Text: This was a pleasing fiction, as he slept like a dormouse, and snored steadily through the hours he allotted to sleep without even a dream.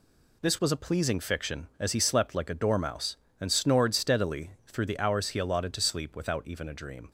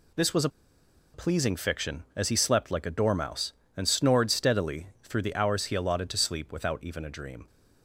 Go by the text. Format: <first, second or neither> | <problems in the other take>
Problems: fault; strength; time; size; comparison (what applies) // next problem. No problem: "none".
first | pauses between "a" and "pleasing"; noticeable; at 0.4 s; 0.64 s long